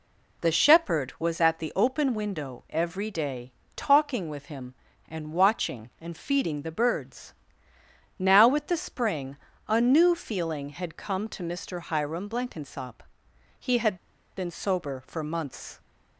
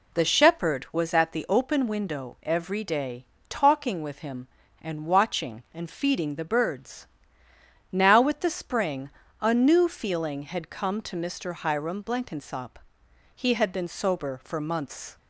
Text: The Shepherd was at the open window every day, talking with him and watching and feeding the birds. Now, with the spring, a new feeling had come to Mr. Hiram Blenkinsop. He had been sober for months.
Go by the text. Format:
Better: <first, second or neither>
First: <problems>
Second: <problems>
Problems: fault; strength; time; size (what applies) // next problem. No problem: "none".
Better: second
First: pauses between "had" and "been"; at 13.9 s; 0.41 s long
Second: none